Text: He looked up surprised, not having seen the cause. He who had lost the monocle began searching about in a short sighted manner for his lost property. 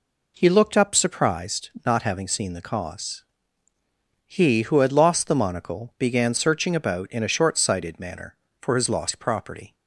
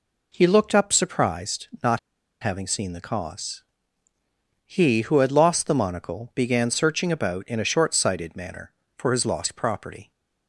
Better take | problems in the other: first | pauses between "not" and "having"; at 1.9 s; 0.42 s long

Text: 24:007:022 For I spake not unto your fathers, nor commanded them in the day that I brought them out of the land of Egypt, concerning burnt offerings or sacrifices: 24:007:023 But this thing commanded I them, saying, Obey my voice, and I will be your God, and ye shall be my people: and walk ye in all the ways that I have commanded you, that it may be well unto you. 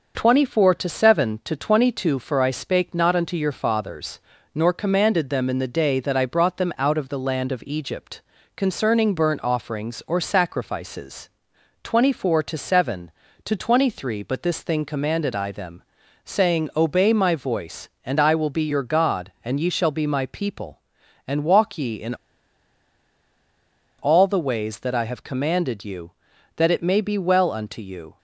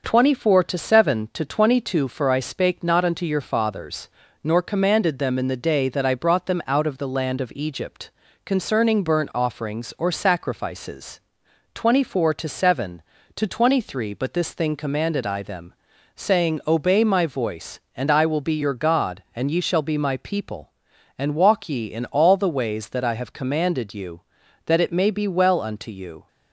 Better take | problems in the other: second | pauses between "in" and "all"; strong; at 22.1 s; 1.8 s long

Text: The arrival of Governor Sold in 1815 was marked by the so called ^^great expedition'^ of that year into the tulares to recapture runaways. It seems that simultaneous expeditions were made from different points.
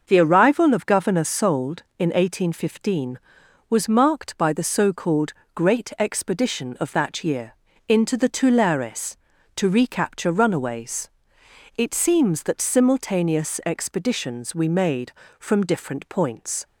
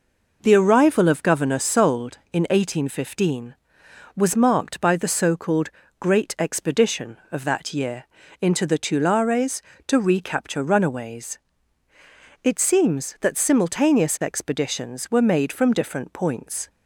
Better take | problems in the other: second | starts louder than the rest; until 1.0 s; 6.5 dB // pauses between "called" and "great"; slight; at 5.3 s; 0.22 s long; slight in the second // pauses between "year" and "into"; slight; at 7.5 s; 0.32 s long; slight in the second // says "we" for "were"; at 14.5 s

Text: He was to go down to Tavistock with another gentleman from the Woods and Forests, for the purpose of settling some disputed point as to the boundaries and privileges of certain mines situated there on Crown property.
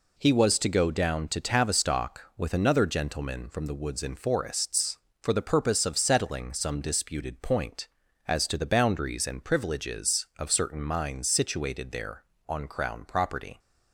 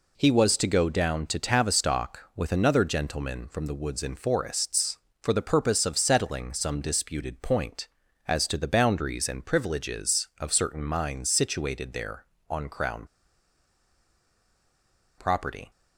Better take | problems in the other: first | pauses between "Crown" and "property"; strong; at 13.0 s; 2.1 s long

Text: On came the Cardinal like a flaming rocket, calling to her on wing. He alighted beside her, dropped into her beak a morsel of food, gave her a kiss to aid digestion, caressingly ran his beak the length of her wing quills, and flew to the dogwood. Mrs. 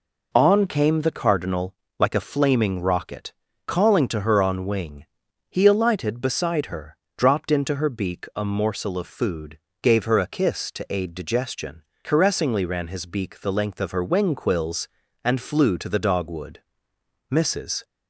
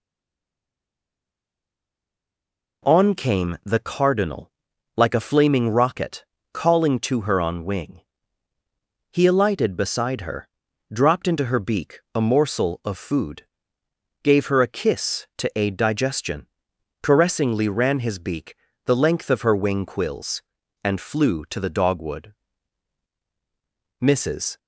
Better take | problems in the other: first | stays silent before the first word; strong; until 2.8 s; 2.8 s long // pauses between "Cardinal" and "like"; noticeable; at 4.4 s; 0.46 s long; slight in the first // pauses between "beak" and "the"; slight; at 18.5 s; 0.32 s long

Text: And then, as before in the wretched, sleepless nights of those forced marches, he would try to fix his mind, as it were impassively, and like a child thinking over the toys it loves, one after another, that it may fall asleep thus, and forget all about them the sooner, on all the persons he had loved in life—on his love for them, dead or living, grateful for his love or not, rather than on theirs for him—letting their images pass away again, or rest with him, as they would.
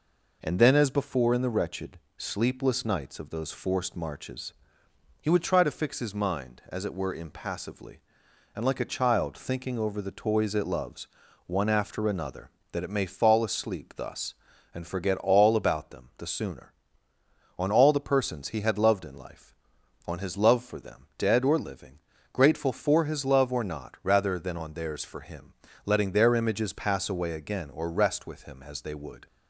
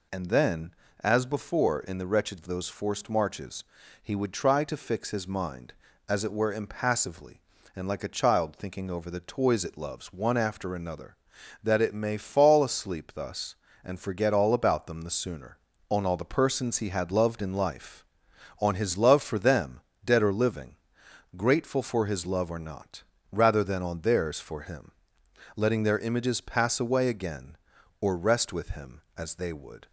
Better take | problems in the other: first | skips "sleepless nights"; at 2.3 s

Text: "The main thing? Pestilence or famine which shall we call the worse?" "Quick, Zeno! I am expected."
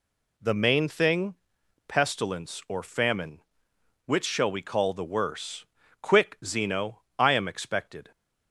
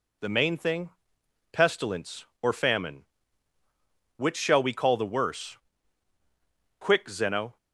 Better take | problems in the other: first | stops before "I am expected"; at 7.5 s

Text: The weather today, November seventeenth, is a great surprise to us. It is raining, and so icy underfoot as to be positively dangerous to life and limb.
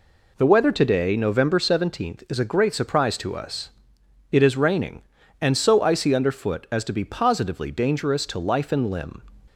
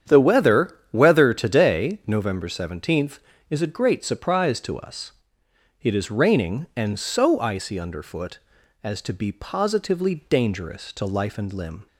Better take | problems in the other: first | starts louder than the rest; strong; until 1.2 s; 9 dB // says "weather" twice; at 0.9 s

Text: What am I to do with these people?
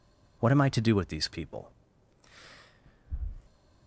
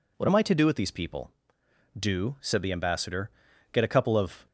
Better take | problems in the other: first | goes on to say "Do said the Ambassador get a couple of"; strong; from 1.9 s on; 2.4 s long

